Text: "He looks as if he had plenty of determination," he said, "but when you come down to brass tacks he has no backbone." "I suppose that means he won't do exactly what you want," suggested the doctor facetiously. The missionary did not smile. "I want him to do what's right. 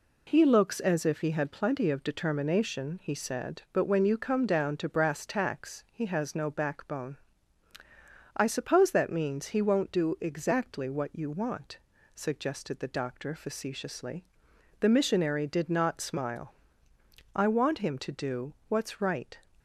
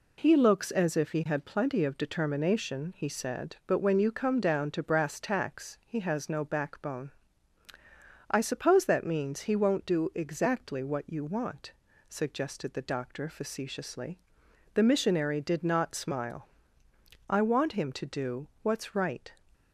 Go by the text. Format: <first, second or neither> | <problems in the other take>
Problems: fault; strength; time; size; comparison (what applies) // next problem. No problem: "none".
neither | none